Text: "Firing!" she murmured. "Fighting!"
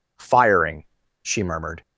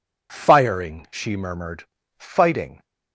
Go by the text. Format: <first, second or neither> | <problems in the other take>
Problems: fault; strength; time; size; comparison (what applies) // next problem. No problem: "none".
second | stops before "Fighting"; at 1.8 s